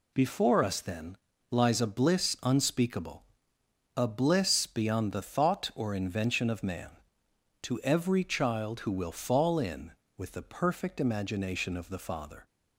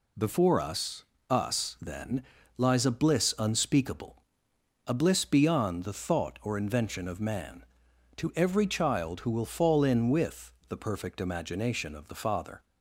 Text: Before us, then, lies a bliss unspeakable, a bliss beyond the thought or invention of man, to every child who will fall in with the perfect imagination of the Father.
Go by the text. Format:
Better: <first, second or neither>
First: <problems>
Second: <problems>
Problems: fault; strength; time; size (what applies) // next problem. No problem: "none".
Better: first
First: none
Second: says "us" twice; at 1.2 s // pauses between "with" and "the"; slight; at 10.5 s; 0.16 s long